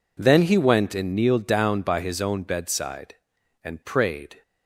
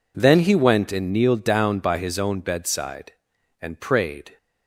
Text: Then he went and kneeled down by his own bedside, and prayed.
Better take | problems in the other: neither | none

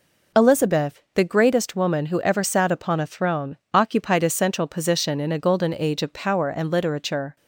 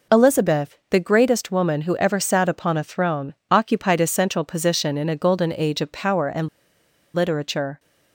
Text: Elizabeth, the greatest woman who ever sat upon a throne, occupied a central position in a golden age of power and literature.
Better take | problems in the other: first | pauses between "and" and "literature"; noticeable; at 6.4 s; 0.65 s long

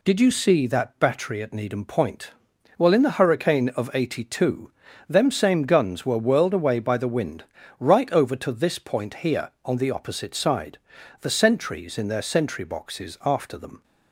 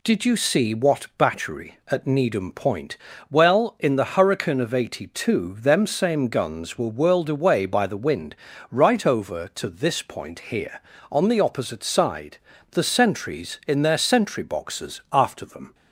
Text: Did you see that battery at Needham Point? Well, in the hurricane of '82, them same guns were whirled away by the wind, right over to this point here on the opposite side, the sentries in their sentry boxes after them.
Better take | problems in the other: first | says "what" for "that"; at 0.7 s

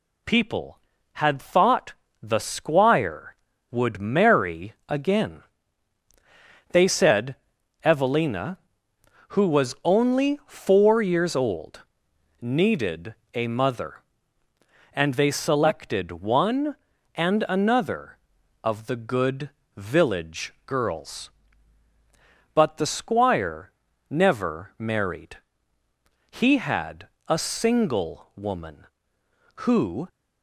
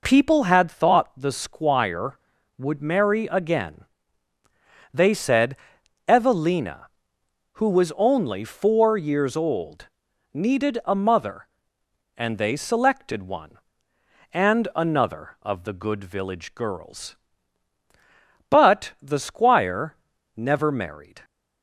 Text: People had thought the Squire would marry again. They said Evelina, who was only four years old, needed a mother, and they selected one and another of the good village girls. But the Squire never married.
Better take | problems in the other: second | pauses between "thought" and "the"; slight; at 1.9 s; 0.28 s long // pauses between "said" and "Evelina"; noticeable; at 7.3 s; 0.48 s long; noticeable in the second // pauses between "needed" and "a"; slight; at 13.1 s; 0.20 s long // pauses between "good" and "village"; slight; at 19.4 s; 0.26 s long // pauses between "Squire" and "never"; at 23.7 s; 0.38 s long; also in the second // goes on to say "He had a single woman who"; strong; from 26.2 s on; 3.7 s long

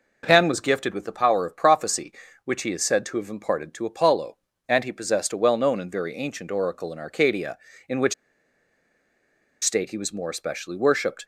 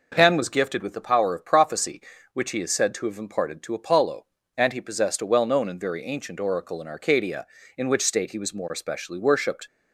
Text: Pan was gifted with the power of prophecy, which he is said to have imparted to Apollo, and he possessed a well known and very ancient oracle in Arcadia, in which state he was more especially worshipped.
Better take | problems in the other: second | pauses between "which" and "state"; strong; at 8.1 s; 1.4 s long

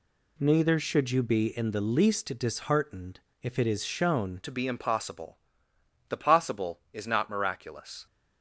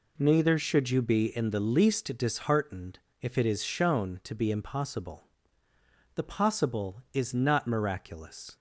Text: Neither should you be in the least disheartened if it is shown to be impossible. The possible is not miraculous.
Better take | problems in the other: second | pauses between "disheartened" and "if"; slight; at 3.2 s; 0.20 s long; slight in the second // changes voice at "to"; from 4.4 s on; 3.6 s long

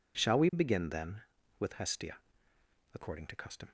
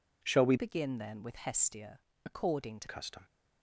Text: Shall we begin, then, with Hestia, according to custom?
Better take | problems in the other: first | changes voice from "begin" to "to"; from 0.5 to 2.8 s; 2.3 s long

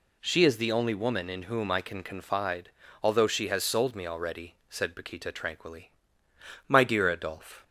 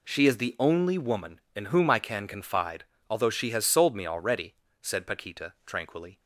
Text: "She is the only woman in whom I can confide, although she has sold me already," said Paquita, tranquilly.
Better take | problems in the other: second | goes on to say "My dear Adolphe"; noticeable; from 6.6 s on; 0.96 s long

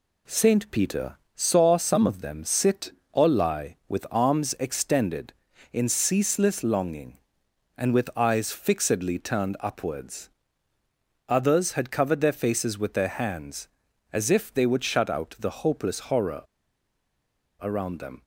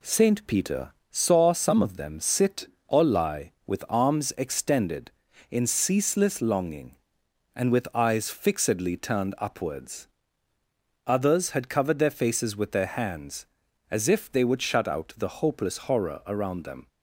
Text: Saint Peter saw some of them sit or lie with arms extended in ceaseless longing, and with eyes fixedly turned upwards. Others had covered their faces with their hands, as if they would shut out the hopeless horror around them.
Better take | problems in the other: second | pauses between "Peter" and "saw"; slight; at 1.1 s; 0.18 s long; slight in the second // pauses between "horror" and "around"; at 16.4 s; 1.1 s long

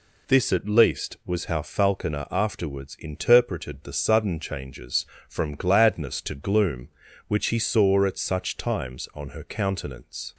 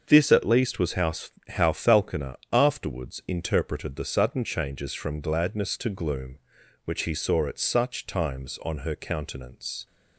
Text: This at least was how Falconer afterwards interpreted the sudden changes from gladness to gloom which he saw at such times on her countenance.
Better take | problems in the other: first | starts louder than the rest; until 1.0 s; 7 dB // says "how" twice; at 1.4 s // pauses between "Falconer" and "afterwards"; slight; at 2.3 s; 0.16 s long

